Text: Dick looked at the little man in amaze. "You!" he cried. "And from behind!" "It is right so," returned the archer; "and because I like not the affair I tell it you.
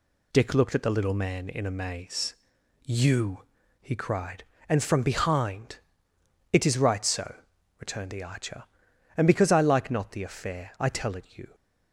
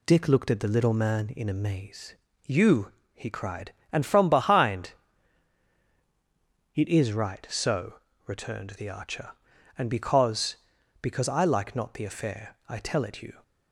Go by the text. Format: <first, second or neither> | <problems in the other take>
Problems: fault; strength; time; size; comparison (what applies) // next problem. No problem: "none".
first | says "because" twice; at 11.0 s